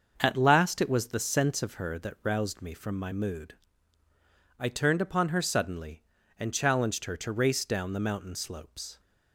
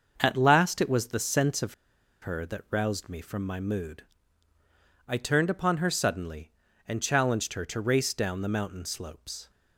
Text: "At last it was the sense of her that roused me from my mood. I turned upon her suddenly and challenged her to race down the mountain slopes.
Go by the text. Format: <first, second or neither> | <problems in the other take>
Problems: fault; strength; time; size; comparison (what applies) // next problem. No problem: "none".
first | starts louder than the rest; until 1.1 s; 6.5 dB; also in the first // pauses between "of" and "her"; noticeable; at 1.7 s; 0.47 s long